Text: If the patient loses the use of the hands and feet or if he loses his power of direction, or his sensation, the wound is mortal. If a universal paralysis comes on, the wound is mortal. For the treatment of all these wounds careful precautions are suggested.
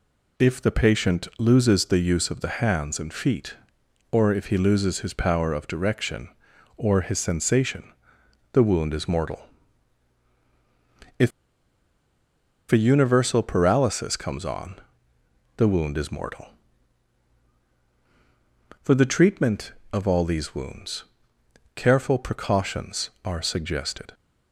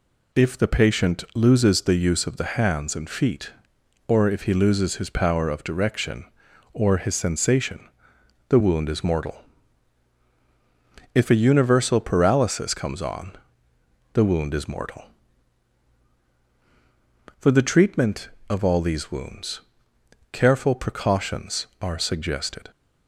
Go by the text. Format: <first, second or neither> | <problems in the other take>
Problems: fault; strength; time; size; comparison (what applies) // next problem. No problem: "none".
second | pauses between "If" and "a"; strong; at 11.3 s; 1.4 s long // pauses between "wounds" and "careful"; noticeable; at 21.0 s; 0.72 s long; noticeable in the second